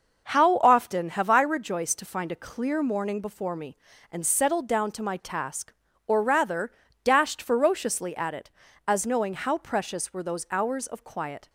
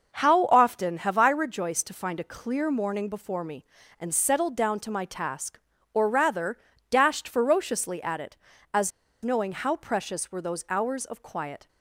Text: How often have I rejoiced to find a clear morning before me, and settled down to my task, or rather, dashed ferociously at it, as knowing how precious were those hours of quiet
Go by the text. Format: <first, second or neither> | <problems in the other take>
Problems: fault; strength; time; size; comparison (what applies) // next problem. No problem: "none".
first | pauses between "as" and "knowing"; slight; at 8.9 s; 0.33 s long